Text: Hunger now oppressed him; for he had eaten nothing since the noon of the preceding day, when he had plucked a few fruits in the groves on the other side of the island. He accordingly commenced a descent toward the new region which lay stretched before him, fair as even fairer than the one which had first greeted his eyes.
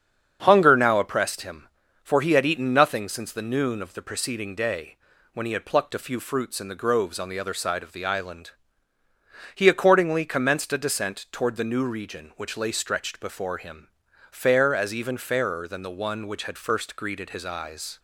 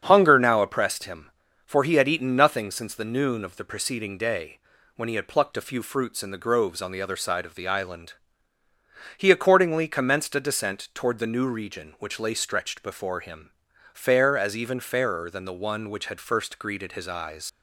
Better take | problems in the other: first | starts louder than the rest; strong; until 1.0 s; 7.5 dB; strong in the first // leaves "eyes" unfinished; at 17.4 s; 120 ms

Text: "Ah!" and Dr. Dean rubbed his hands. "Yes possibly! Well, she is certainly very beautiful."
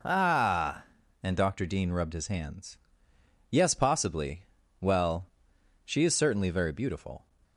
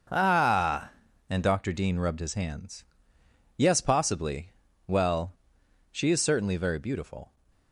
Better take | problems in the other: first | gets quieter; strong; throughout; 10 dB

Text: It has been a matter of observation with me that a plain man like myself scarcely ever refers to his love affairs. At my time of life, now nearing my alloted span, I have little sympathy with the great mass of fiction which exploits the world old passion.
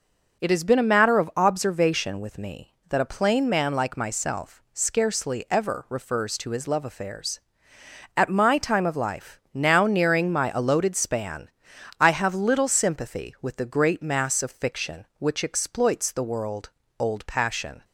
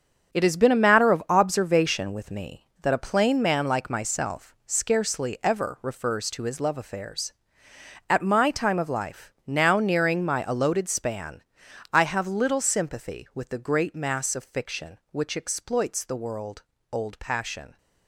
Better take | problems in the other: first | gets quieter; strong; throughout; 9.5 dB // starts louder than the rest; strong; until 1.3 s; 7.5 dB; also in the first // pauses between "world" and "old"; slight; at 16.6 s; 0.28 s long; slight in the first

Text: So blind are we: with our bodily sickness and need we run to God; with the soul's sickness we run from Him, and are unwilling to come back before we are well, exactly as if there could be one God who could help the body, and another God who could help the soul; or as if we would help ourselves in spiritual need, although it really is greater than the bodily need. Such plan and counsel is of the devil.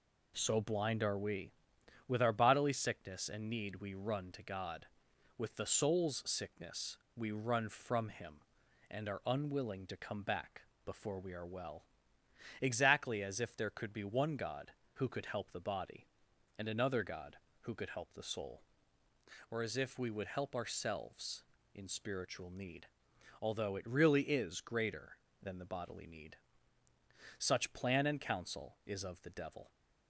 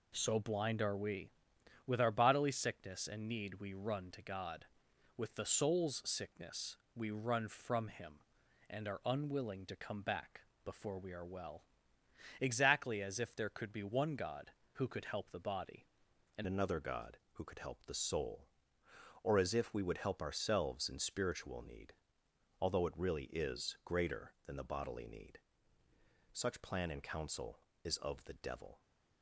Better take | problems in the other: first | pauses between "sickness" and "we"; slight; at 6.7 s; 0.18 s long; slight in the first // pauses between "back" and "before"; slight; at 10.4 s; 0.22 s long; slight in the first // changes voice at "another"; from 16.4 s on; 12.4 s long

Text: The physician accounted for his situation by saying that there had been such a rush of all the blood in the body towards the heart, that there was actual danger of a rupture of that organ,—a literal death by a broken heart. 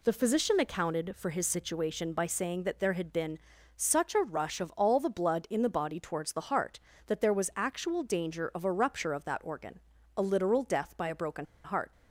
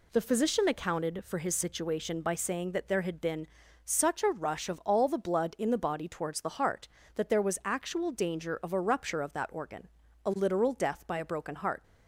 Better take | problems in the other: second | pauses between "been" and "such"; at 3.3 s; 0.40 s long; also in the second // pauses between "broken" and "heart"; slight; at 11.4 s; 0.19 s long

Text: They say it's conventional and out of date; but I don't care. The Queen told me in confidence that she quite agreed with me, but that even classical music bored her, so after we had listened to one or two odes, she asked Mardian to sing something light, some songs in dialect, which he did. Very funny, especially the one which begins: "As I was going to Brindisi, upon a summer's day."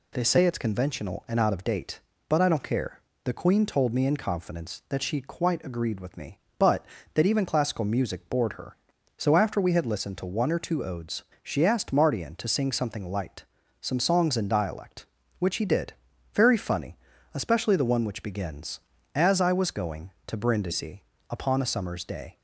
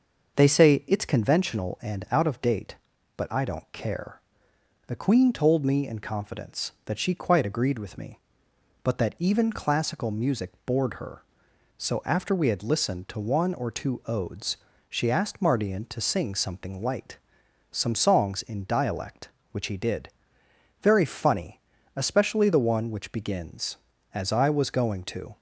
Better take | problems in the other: first | starts louder than the rest; until 1.4 s; 6 dB // pauses between "music" and "bored"; slight; at 10.5 s; 0.16 s long // stops before "Brindisi upon a summer's day"; at 25.3 s

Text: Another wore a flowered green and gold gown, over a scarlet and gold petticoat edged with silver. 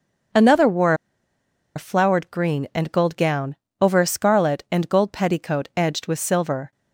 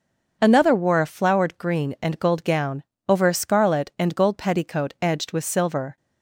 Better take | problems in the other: second | starts louder than the rest; until 2.1 s; 6.5 dB; also in the second // pauses between "wore" and "a"; noticeable; at 0.9 s; 0.81 s long

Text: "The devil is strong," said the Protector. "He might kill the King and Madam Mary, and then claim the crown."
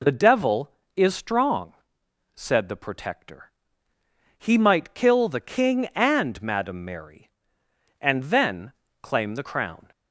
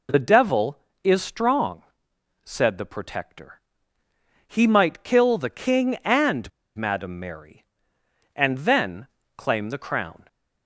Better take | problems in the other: first | pauses between "and" and "Madam"; slight; at 6.4 s; 0.25 s long // pauses between "then" and "claim"; slight; at 9.0 s; 0.30 s long; slight in the first

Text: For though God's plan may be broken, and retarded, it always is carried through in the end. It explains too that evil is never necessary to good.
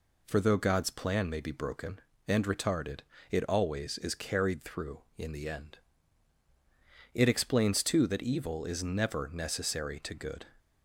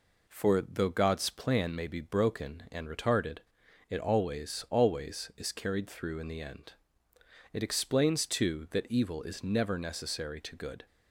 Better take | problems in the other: first | says "always" twice; at 4.6 s

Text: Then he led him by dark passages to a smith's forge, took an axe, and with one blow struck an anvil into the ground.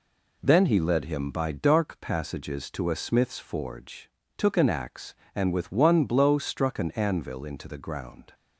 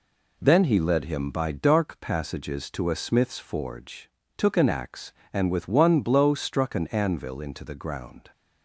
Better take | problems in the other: neither | none

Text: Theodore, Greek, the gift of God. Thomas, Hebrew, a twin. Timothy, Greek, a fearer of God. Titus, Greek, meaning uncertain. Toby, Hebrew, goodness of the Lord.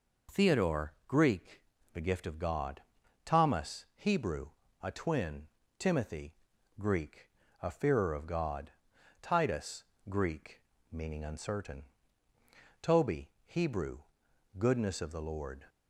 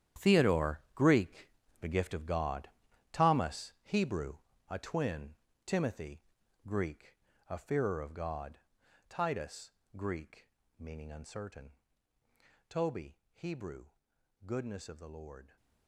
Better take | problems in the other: first | gets quieter; strong; throughout; 13.5 dB

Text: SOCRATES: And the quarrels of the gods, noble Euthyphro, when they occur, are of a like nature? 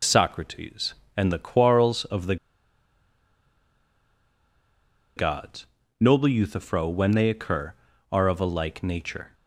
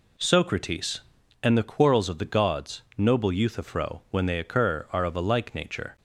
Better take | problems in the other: second | pauses between "the" and "gods"; strong; at 2.3 s; 2.8 s long

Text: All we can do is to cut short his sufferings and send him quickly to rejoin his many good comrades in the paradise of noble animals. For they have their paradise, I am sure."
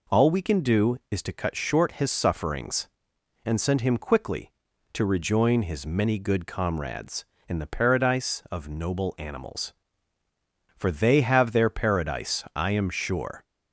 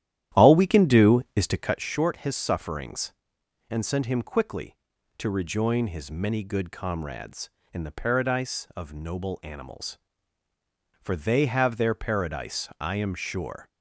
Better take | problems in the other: first | starts louder than the rest; strong; until 1.9 s; 12 dB

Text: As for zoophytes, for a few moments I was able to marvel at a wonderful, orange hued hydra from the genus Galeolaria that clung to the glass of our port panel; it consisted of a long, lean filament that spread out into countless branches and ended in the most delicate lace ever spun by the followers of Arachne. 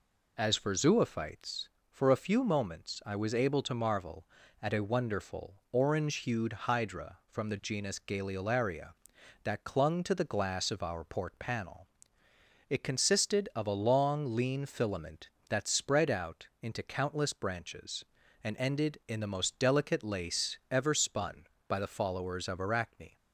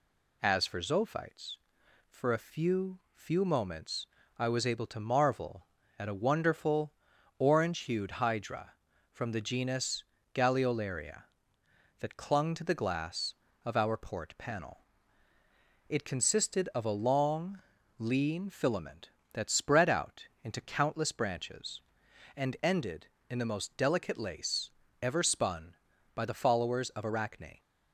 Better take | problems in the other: first | says "few" twice; at 3.1 s // pauses between "moments" and "I"; slight; at 4.0 s; 0.30 s long // pauses between "genus" and "Galeolaria"; slight; at 10.0 s; 0.32 s long // pauses between "out" and "into"; slight; at 20.2 s; 0.16 s long // pauses between "lace" and "ever"; slight; at 24.6 s; 0.32 s long

